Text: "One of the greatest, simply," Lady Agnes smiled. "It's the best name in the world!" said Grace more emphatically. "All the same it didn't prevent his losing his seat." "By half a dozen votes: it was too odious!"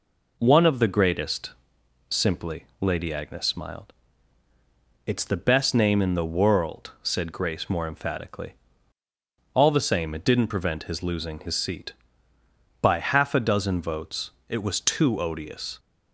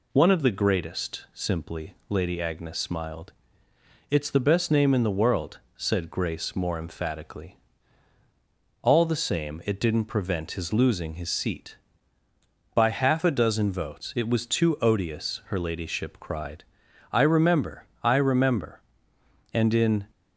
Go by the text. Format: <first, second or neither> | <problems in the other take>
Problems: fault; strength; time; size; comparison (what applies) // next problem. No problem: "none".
first | goes on to say "her ladyship cried I remember I remember And in"; strong; from 15.4 s on; 4.6 s long